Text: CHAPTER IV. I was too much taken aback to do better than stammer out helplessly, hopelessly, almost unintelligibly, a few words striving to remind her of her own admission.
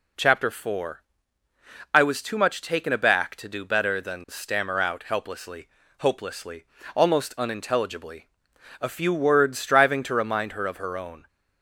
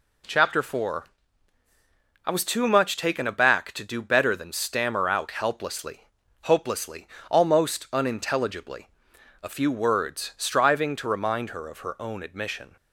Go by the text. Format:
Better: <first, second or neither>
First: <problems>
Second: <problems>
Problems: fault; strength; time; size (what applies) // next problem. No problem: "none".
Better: second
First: stops before "admission"; at 11.2 s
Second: none